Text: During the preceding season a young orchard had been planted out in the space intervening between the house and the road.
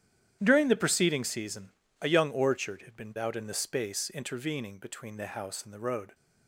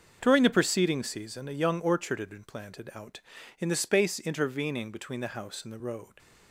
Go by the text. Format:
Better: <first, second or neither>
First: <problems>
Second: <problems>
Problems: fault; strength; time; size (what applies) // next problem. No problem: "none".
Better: second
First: starts louder than the rest; strong; until 1.4 s; 10.5 dB // pauses between "season" and "a"; slight; at 1.7 s; 0.28 s long // skips "planted"; at 3.1 s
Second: starts louder than the rest; until 1.2 s; 6.5 dB